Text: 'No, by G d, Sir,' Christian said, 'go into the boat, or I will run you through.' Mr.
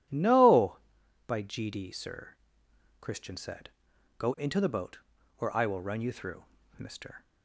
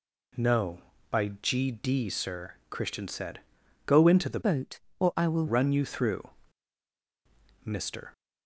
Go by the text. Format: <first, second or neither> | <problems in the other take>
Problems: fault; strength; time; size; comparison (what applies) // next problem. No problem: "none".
first | changes voice from "boat" to "will"; from 4.4 to 5.4 s; 1.0 s long